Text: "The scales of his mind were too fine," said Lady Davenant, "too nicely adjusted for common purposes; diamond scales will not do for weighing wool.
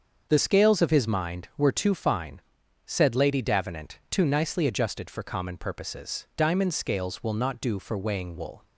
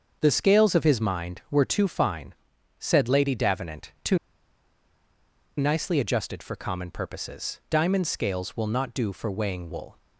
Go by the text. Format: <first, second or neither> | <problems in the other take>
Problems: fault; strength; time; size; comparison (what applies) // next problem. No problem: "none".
first | starts louder than the rest; until 1.2 s; 6.5 dB; also in the first // pauses between "too" and "nicely"; strong; at 4.1 s; 1.4 s long